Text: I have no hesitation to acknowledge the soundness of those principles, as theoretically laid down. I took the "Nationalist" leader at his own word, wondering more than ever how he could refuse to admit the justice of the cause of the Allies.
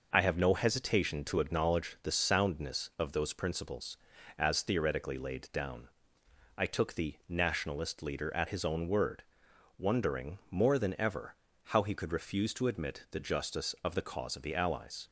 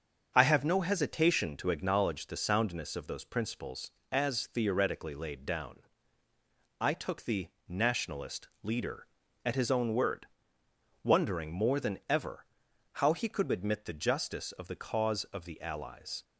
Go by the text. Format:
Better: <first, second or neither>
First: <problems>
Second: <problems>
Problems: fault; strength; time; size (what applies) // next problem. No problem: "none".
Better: first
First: pauses between "ever" and "how"; slight; at 11.3 s; 0.30 s long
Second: starts louder than the rest; until 1.3 s; 6.5 dB // pauses between "the" and "Nationalist"; slight; at 7.4 s; 0.20 s long // pauses between "Nationalist" and "leader"; slight; at 8.4 s; 0.16 s long // pauses between "ever" and "how"; noticeable; at 12.4 s; 0.48 s long // skips "refuse to"; at 13.5 s